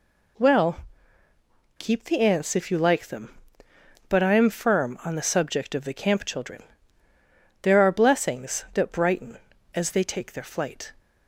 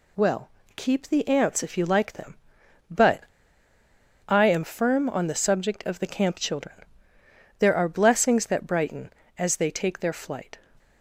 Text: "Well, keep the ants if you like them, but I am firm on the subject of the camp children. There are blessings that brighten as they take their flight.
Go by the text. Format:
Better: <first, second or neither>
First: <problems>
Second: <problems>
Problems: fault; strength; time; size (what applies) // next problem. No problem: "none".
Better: first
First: none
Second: pauses between "but" and "I"; at 3.2 s; 1.0 s long